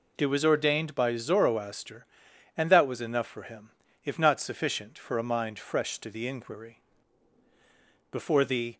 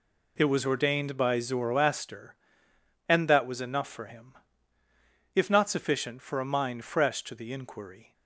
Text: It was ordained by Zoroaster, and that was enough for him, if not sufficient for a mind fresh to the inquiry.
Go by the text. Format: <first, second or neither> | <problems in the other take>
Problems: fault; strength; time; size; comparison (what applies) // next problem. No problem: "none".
second | goes on to say "Before the"; noticeable; from 8.1 s on; 0.66 s long